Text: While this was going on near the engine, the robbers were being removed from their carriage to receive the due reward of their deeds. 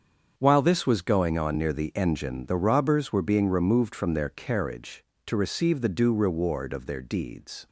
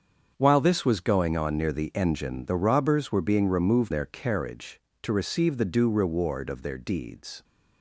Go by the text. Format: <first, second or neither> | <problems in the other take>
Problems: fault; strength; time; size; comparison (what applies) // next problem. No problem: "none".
first | starts louder than the rest; until 1.3 s; 7 dB; strong in the first // skips "from"; at 3.9 s